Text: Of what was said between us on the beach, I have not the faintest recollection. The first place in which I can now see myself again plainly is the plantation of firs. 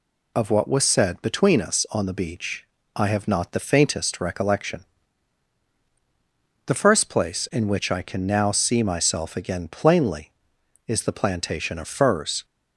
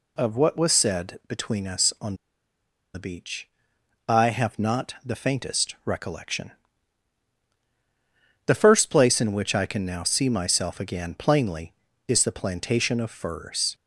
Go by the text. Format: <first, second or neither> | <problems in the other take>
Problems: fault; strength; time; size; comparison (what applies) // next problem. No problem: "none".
first | pauses between "on" and "the"; noticeable; at 2.1 s; 0.79 s long